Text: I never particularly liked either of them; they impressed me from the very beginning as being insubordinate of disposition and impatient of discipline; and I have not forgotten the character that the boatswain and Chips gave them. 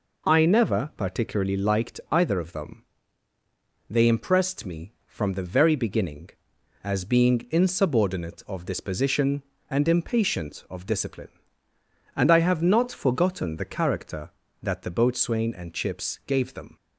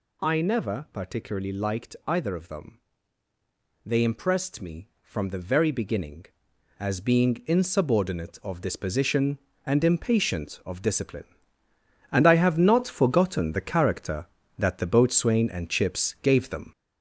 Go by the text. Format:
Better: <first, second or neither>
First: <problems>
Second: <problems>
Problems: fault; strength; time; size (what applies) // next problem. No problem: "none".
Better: first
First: none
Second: gets louder; noticeable; throughout; 5 dB